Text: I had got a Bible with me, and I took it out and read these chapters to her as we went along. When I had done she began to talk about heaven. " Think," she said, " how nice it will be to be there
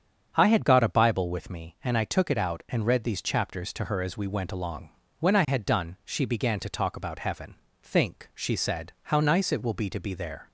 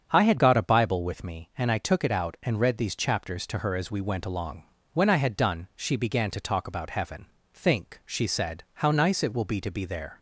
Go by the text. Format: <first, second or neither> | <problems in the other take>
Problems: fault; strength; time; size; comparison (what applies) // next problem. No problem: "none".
neither | starts louder than the rest; strong; the same in both